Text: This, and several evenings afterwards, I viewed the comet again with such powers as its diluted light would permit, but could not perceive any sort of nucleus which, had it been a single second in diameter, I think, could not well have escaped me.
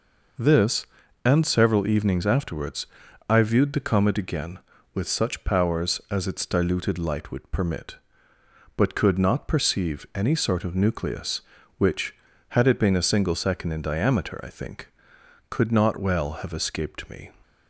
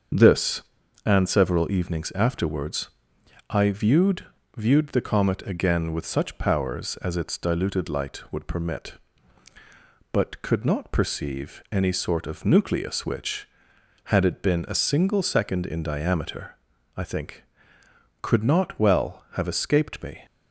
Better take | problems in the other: first | starts louder than the rest; until 1.5 s; 6.5 dB // says "viewed" twice; at 4.5 s

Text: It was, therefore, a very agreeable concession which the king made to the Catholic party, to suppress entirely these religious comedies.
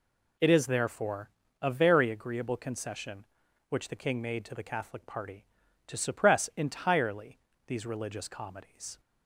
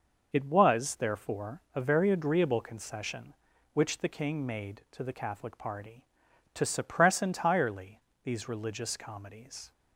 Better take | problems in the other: second | says "is" for "was"; at 0.4 s // pauses between "entirely" and "these"; slight; at 7.3 s; 0.26 s long; slight in the second

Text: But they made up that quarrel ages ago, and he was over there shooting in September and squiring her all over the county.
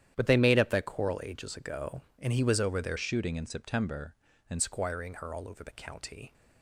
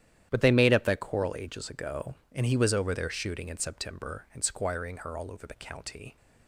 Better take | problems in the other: second | starts louder than the rest; strong; until 1.1 s; 10.5 dB; strong in the second // changes voice from "shooting" to "and"; from 2.9 to 4.6 s; 1.7 s long

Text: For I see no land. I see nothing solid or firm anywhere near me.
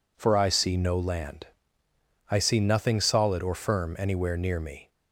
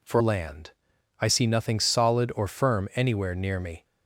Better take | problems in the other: first | skips "I see no"; at 0.2 s

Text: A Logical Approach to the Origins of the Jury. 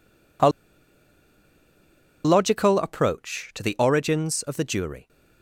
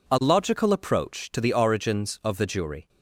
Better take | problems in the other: second | pauses between "A" and "Logical"; strong; at 0.4 s; 1.7 s long

